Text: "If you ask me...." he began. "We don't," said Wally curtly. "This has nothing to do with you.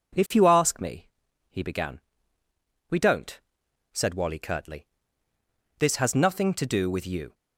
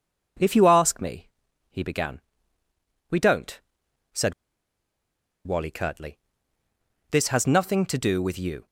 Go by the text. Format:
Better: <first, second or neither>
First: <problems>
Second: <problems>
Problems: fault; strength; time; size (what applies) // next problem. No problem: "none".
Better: first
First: none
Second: pauses between "said" and "Wally"; at 4.3 s; 1.1 s long